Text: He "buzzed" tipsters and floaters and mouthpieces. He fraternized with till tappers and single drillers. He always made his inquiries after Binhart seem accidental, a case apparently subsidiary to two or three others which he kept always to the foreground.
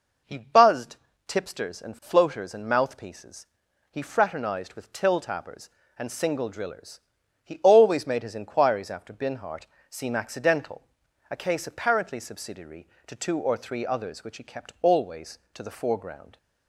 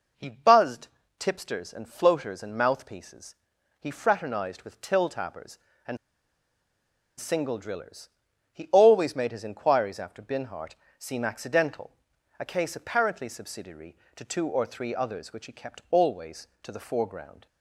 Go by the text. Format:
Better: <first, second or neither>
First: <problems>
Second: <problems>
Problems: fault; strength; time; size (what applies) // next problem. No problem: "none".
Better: first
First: pauses between "buzzed" and "tipsters"; slight; at 0.9 s; 0.30 s long // pauses between "Binhart" and "seem"; slight; at 9.6 s; 0.22 s long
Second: pauses between "buzzed" and "tipsters"; slight; at 0.8 s; 0.30 s long // pauses between "and" and "single"; at 5.9 s; 1.2 s long // pauses between "Binhart" and "seem"; slight; at 10.7 s; 0.22 s long